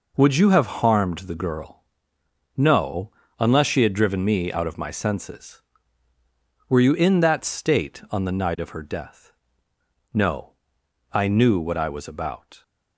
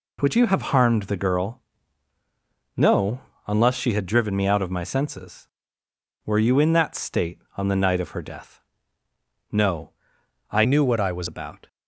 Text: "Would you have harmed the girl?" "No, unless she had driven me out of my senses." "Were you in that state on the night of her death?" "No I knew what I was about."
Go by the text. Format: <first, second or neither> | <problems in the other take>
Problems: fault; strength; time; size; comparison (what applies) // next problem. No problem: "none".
first | pauses between "No" and "I"; noticeable; at 9.9 s; 0.58 s long; noticeable in the first // changes voice from "knew" to "was"; from 10.6 to 11.2 s; 0.6 s long